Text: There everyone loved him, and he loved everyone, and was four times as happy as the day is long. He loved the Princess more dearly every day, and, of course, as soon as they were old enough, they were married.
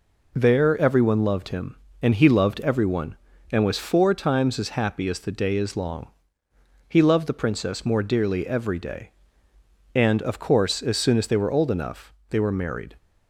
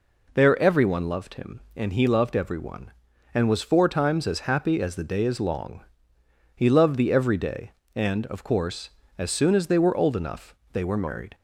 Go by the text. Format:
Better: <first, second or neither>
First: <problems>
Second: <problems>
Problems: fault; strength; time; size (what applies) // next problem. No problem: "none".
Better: first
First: none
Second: skips "Princess more dearly"; at 7.1 s